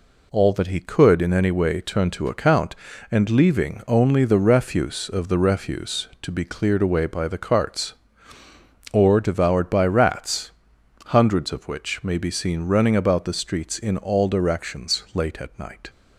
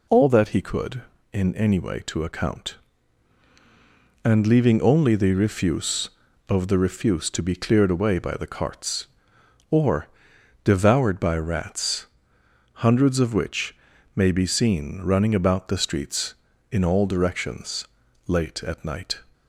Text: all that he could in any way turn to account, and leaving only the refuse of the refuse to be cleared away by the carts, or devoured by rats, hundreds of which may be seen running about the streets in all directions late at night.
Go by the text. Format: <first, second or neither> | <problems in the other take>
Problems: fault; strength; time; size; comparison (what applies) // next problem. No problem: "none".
first | skips "turn"; at 2.0 s // pauses between "or" and "devoured"; noticeable; at 10.0 s; 0.56 s long // pauses between "which" and "may"; at 13.7 s; 0.40 s long // pauses between "directions" and "late"; at 17.8 s; 0.40 s long